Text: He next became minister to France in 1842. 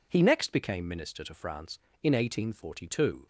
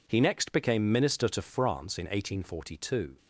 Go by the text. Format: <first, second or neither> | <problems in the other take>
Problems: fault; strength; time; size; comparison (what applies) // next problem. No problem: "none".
neither | none